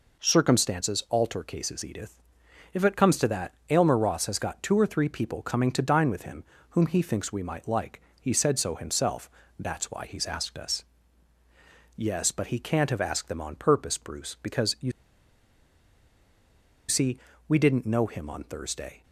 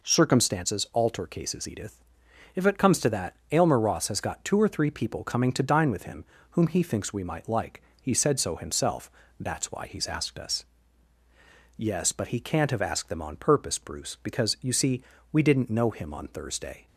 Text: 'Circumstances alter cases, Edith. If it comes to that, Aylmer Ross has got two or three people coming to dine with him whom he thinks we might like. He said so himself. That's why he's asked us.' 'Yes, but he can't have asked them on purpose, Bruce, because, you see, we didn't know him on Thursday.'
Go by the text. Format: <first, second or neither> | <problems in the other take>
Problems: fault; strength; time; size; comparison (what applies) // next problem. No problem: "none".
second | pauses between "him" and "whom"; slight; at 6.4 s; 0.26 s long; slight in the second // pauses between "you" and "see"; strong; at 14.8 s; 1.9 s long